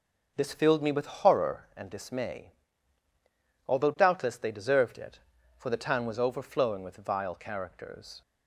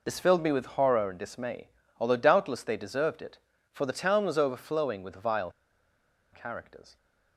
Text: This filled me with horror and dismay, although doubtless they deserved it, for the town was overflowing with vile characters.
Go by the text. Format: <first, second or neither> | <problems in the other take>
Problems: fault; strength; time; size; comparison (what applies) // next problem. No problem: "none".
first | pauses between "vile" and "characters"; noticeable; at 5.4 s; 0.82 s long